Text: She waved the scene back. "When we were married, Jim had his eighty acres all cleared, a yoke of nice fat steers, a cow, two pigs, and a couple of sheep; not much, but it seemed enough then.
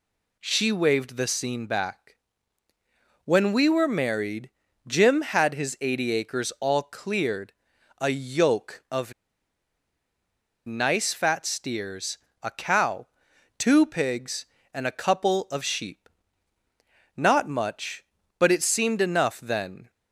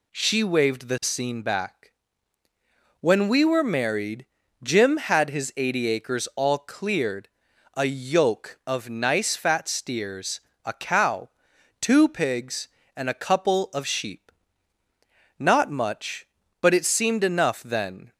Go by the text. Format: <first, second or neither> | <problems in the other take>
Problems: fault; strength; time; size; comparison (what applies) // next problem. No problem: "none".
second | pauses between "of" and "nice"; strong; at 9.1 s; 1.5 s long